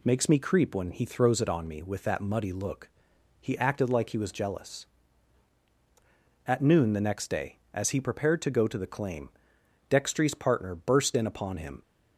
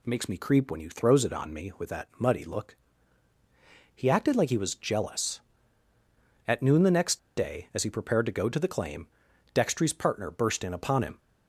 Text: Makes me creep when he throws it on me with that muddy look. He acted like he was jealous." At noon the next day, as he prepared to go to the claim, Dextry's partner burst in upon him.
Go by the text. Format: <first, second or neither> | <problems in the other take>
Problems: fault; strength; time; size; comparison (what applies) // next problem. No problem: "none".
first | pauses between "next" and "day"; slight; at 7.1 s; 0.17 s long